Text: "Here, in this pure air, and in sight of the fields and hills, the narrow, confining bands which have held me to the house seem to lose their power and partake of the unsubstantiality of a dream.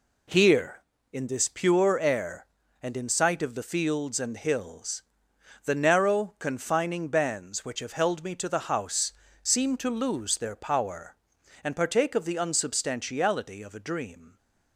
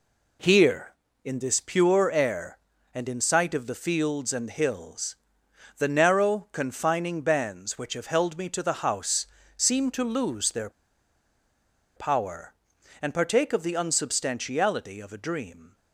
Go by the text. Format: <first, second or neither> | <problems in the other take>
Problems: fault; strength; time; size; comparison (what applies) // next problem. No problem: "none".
first | pauses between "house" and "seem"; slight; at 9.2 s; 0.28 s long; slight in the first // pauses between "their" and "power"; strong; at 10.7 s; 1.2 s long